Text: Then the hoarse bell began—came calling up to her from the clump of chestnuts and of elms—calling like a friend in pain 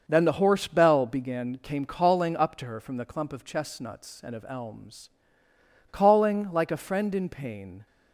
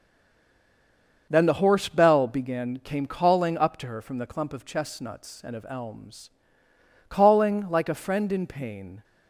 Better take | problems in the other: first | stays silent before the first word; noticeable; until 1.2 s; 1.2 s long // starts louder than the rest; until 2.3 s; 6.5 dB; also in the first

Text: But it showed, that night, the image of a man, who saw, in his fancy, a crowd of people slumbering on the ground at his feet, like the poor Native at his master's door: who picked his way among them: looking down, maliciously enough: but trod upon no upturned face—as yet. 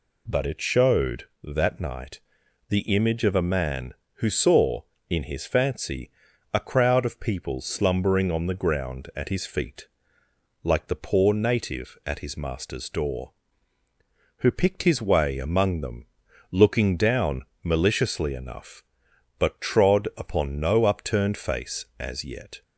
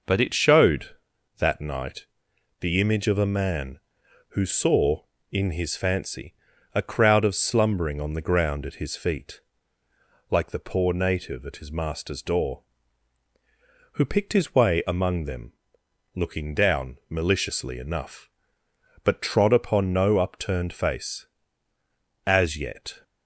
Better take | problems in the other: first | skips "people"; at 7.3 s

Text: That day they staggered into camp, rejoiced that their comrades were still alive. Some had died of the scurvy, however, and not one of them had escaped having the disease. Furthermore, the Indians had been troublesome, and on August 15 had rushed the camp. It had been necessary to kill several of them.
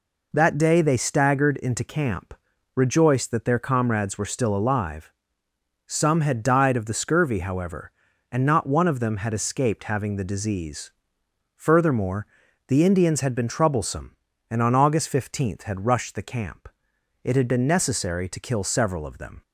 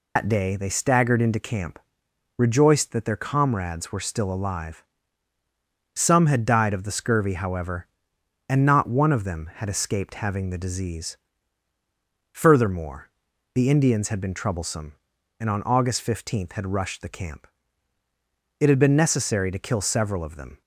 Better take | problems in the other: first | loses the start of "That"; at 0.1 s; 105 ms

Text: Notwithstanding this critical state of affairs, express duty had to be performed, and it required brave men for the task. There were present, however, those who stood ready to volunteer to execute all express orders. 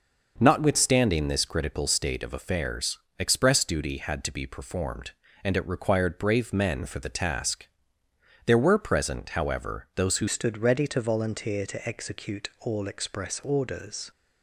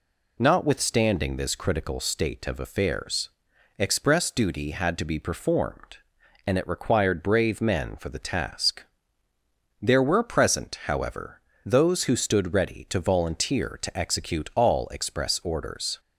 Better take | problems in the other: second | changes voice at "stood"; from 10.2 s on; 3.9 s long

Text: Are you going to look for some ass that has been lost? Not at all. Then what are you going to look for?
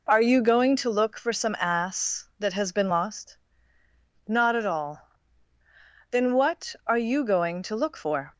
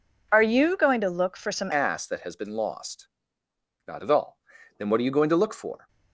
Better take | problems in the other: first | changes voice at "ass"; from 1.7 s on; 4.1 s long

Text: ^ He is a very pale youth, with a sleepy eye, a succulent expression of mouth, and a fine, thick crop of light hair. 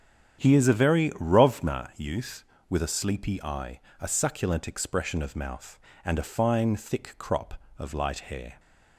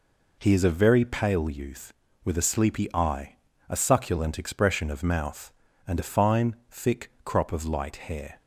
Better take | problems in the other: second | starts louder than the rest; strong; until 1.5 s; 9 dB // says "rovna" for "pale"; at 1.1 s

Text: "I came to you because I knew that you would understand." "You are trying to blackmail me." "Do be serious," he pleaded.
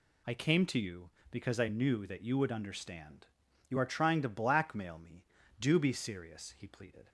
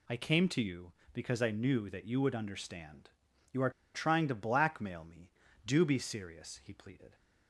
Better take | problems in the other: first | pauses between "are" and "trying"; slight; at 3.7 s; 0.23 s long

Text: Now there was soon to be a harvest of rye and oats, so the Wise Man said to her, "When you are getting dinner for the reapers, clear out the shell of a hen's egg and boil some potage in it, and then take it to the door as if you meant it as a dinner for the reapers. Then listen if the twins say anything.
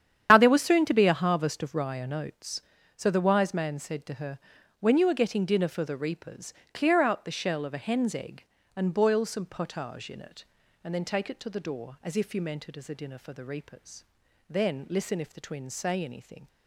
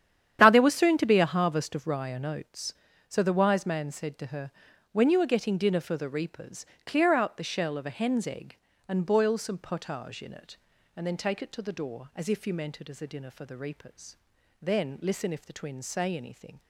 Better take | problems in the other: second | loses the start of "Now"; at 0.2 s; 30 ms // starts louder than the rest; strong; until 1.3 s; 9.5 dB; strong in the second

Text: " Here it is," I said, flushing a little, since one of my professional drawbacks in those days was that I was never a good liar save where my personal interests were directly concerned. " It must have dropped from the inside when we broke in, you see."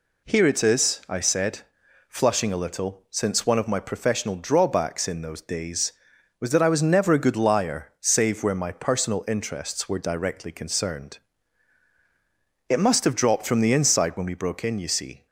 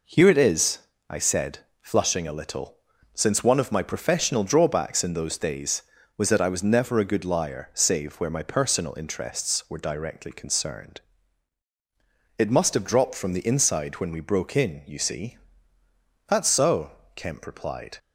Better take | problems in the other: first | goes on to say "That's so Kemp replied"; strong; from 16.2 s on; 1.6 s long

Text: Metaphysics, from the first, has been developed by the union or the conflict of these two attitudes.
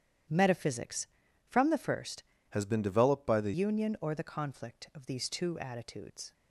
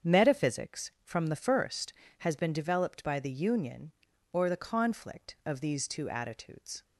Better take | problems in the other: second | starts louder than the rest; strong; until 1.7 s; 10 dB; strong in the second // changes voice from "has" to "the"; from 2.5 to 3.5 s; 1.0 s long

